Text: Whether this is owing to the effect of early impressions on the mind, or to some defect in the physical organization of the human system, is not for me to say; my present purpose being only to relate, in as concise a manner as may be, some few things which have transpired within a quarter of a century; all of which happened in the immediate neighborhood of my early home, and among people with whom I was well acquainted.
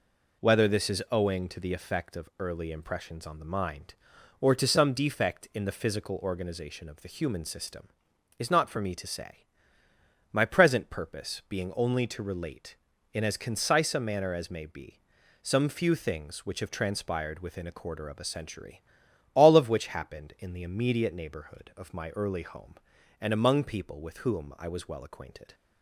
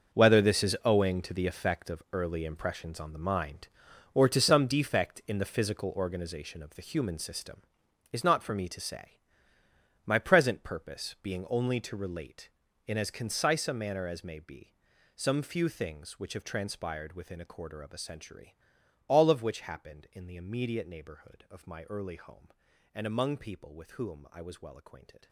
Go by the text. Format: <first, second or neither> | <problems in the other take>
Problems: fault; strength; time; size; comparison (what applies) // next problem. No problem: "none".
first | gets quieter; strong; throughout; 14 dB